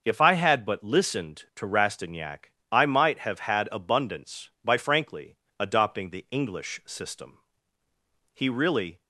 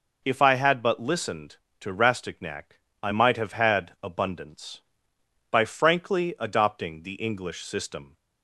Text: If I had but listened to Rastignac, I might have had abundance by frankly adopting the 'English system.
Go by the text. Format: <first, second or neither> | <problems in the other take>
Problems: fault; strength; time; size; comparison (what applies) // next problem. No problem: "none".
second | starts louder than the rest; noticeable; until 1.0 s; 6 dB // pauses between "frankly" and "adopting"; slight; at 5.3 s; 0.24 s long // goes on to say "He really"; noticeable; from 8.3 s on; 0.68 s long